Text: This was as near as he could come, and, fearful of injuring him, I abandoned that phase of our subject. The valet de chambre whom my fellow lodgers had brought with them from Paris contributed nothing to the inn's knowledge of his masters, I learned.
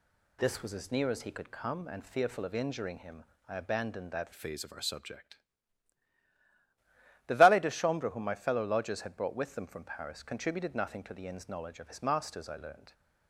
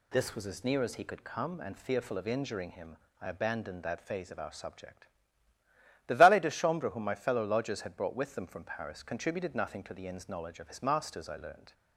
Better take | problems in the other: second | changes voice from "phase" to "subject"; from 4.3 to 5.3 s; 1.0 s long

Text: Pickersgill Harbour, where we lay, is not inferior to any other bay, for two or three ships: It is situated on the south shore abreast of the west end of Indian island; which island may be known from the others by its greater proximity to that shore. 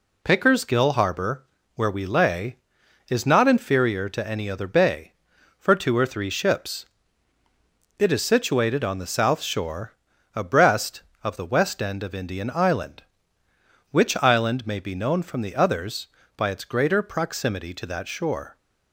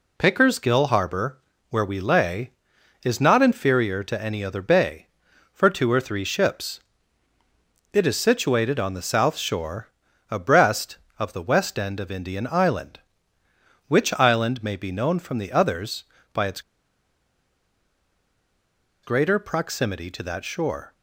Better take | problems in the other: first | pauses between "shore" and "abreast"; at 9.8 s; 0.42 s long; also in the first // pauses between "its" and "greater"; strong; at 16.6 s; 2.4 s long

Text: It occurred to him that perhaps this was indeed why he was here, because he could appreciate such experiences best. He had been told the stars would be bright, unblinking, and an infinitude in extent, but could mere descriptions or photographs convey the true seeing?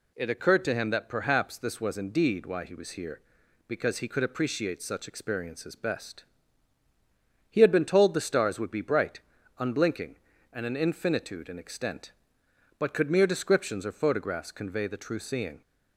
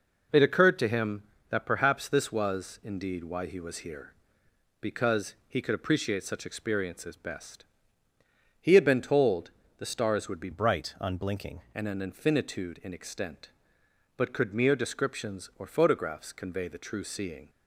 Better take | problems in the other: first | pauses between "told" and "the"; slight; at 9.4 s; 0.28 s long // changes voice from "bright" to "unblinking"; from 10.5 to 11.5 s; 1.0 s long

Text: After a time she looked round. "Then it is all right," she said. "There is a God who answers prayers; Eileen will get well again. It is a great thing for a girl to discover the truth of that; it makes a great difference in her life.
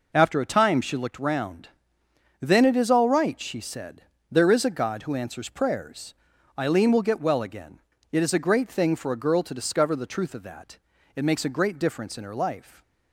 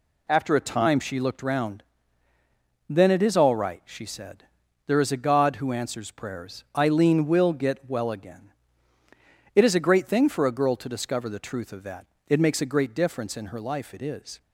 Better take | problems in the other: first | goes on to say "It is"; slight; from 13.9 s on; 0.46 s long

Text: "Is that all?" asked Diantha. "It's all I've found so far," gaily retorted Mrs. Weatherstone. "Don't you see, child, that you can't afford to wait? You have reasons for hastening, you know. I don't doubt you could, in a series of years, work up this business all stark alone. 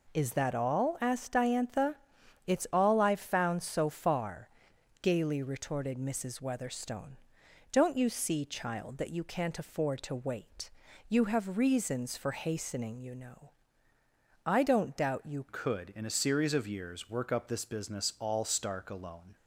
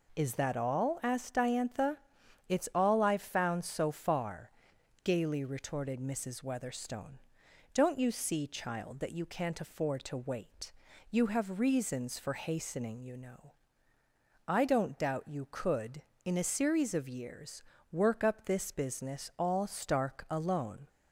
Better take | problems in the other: second | changes voice at "could"; from 15.4 s on; 3.9 s long

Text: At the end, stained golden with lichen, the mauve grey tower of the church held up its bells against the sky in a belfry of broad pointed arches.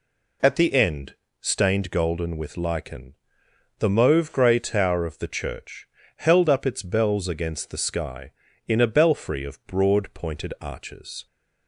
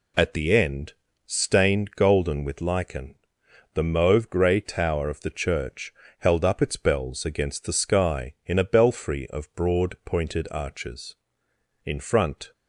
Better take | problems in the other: first | pauses between "church" and "held"; slight; at 5.9 s; 0.24 s long; slight in the first // goes on to say "In front"; noticeable; from 11.8 s on; 0.66 s long

